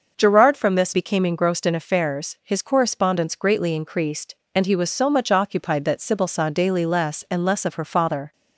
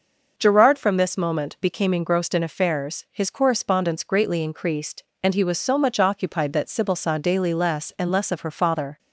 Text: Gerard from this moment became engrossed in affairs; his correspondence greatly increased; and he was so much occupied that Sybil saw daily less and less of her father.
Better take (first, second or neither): second